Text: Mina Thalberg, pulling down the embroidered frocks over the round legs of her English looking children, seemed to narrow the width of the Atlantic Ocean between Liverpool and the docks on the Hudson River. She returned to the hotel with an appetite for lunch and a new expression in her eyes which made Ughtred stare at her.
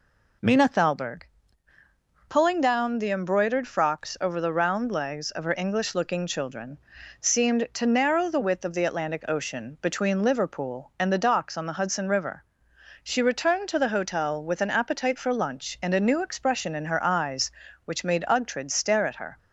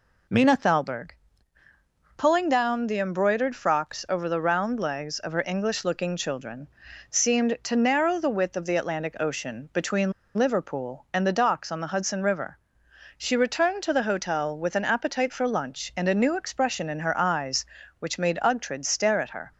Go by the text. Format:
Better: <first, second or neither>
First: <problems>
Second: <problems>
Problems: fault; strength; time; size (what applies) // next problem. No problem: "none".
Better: first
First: none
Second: pauses between "between" and "Liverpool"; slight; at 10.1 s; 0.25 s long